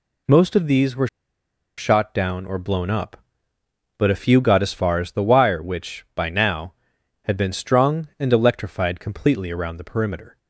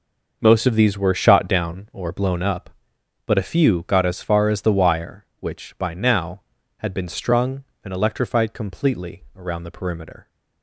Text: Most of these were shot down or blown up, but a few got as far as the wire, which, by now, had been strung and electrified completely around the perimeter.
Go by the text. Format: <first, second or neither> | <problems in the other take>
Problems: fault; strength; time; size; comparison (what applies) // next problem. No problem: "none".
second | pauses between "were" and "shot"; noticeable; at 1.0 s; 0.70 s long